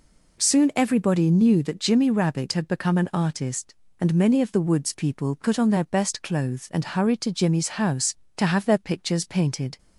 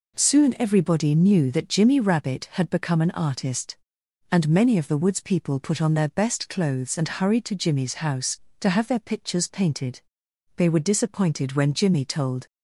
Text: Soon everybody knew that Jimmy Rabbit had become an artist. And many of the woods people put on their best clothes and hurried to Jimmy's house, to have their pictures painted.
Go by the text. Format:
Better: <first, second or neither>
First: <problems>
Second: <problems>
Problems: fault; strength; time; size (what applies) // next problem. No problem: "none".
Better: first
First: none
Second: goes on to say "They were disappointed when Jimmy told"; strong; from 10.5 s on; 1.9 s long